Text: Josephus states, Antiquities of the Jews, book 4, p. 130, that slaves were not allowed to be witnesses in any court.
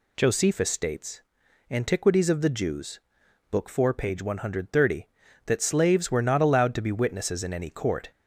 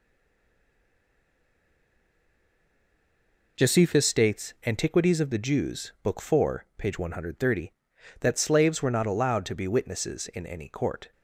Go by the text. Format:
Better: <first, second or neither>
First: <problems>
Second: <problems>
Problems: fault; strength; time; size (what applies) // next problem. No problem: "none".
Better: first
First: none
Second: stays silent before the first word; strong; until 3.5 s; 3.5 s long